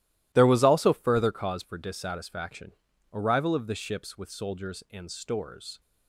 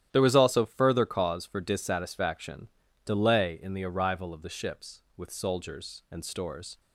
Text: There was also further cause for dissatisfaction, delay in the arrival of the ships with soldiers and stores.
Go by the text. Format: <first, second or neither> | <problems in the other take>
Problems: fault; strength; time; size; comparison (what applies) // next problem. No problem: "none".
second | starts louder than the rest; strong; until 1.3 s; 15 dB; strong in the second // skips "delay in the"; at 2.9 s